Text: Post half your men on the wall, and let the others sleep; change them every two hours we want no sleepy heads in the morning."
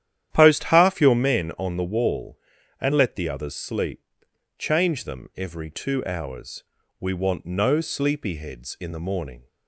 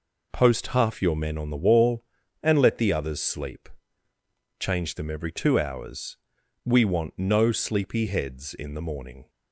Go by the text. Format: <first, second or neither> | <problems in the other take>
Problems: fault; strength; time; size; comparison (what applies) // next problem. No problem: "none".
second | starts louder than the rest; strong; until 1.4 s; 11 dB // pauses between "hours" and "we"; at 6.6 s; 0.38 s long; noticeable in the second